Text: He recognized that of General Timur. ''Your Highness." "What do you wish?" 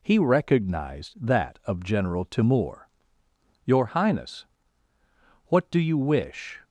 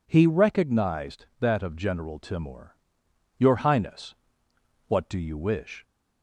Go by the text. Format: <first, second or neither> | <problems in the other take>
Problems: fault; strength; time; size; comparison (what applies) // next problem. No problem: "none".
neither | none